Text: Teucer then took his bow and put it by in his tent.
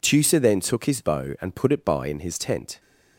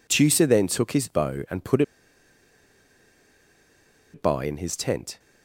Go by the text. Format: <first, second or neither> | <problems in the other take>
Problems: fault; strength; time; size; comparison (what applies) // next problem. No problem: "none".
first | pauses between "put" and "it"; strong; at 1.8 s; 2.3 s long